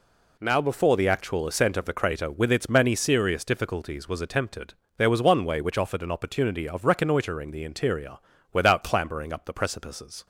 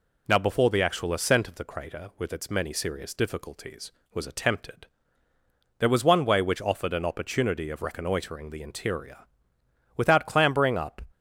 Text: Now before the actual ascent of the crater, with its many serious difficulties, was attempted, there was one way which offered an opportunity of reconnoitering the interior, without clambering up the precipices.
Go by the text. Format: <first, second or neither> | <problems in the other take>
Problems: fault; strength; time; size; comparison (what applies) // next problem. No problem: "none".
first | stops before "the precipices"; at 11.1 s